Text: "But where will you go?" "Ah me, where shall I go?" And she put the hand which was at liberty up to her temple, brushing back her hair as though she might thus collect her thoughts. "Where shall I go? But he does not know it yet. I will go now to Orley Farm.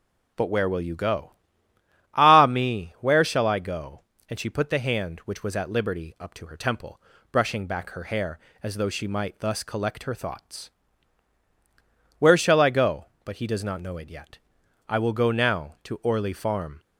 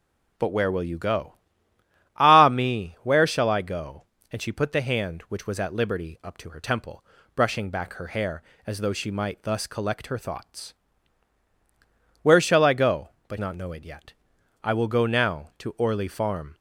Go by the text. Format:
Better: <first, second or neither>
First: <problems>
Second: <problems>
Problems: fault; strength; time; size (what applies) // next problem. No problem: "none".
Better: first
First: none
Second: skips "he does"; at 13.3 s